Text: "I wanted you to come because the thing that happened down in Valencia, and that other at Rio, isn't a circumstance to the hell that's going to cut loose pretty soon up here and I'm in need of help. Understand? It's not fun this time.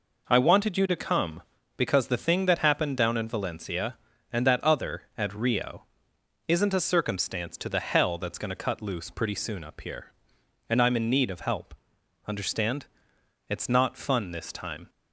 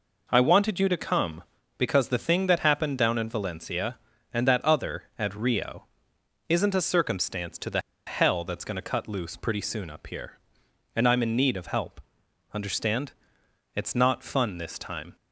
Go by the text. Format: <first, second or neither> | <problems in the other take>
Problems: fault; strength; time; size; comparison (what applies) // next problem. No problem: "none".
first | pauses between "the" and "hell"; slight; at 7.8 s; 0.25 s long